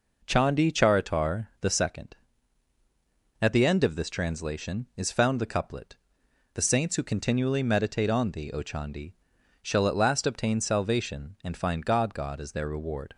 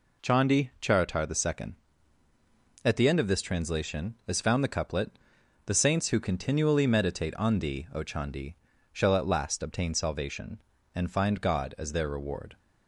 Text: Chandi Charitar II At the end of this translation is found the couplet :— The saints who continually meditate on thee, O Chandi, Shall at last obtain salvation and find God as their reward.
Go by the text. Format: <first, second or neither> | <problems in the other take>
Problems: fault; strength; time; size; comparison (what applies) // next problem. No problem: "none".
second | says "God" twice; at 12.1 s